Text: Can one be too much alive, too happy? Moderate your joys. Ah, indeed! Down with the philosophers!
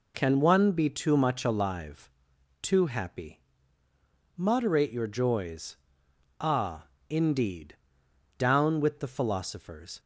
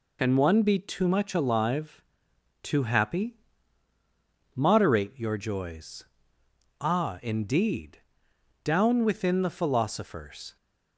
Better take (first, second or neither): first